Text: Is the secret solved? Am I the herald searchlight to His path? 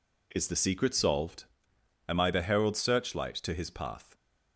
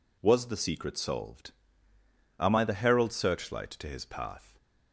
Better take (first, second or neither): first